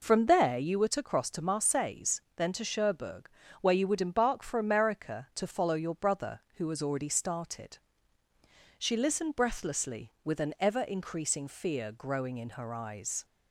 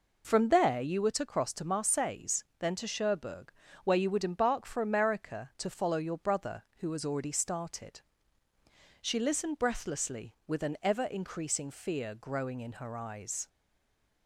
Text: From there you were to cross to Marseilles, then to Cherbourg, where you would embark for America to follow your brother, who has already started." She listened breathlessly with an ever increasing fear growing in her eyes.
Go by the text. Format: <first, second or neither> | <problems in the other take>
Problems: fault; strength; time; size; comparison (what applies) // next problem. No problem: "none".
first | stays silent after the last word; slight; from 13.4 s on; 0.8 s long